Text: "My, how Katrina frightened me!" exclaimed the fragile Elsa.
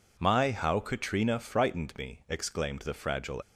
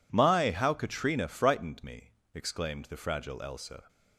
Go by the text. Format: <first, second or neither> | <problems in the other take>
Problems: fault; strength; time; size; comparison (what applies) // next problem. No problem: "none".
second | stops before "Elsa"; at 3.4 s